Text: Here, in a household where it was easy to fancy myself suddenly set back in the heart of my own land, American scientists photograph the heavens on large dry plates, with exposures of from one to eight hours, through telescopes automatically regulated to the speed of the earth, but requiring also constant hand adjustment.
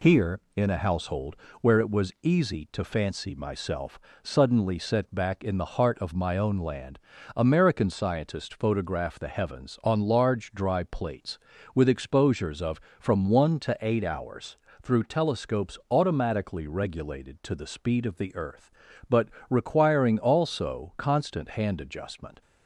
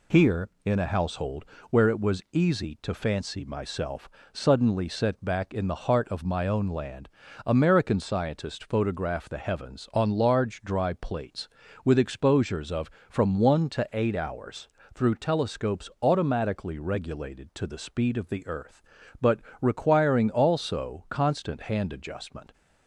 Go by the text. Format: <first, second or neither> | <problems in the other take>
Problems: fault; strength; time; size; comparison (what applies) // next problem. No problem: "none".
neither | pauses between "household" and "where"; slight; the same in both // pauses between "myself" and "suddenly"; slight; the same in both // pauses between "but" and "requiring"; slight; the same in both